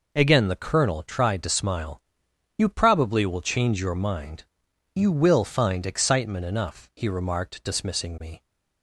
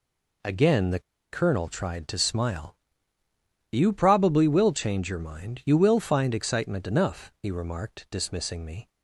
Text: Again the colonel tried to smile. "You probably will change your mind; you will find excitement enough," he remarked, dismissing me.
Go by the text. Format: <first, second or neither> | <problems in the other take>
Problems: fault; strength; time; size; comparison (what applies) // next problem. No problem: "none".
first | pauses between "the" and "colonel"; slight; at 0.9 s; 0.31 s long